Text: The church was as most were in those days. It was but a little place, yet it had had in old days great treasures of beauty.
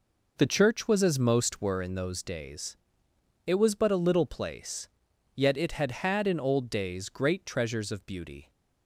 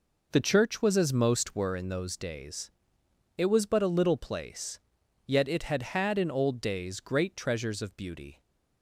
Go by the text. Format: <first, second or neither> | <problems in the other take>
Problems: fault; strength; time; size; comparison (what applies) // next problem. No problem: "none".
neither | none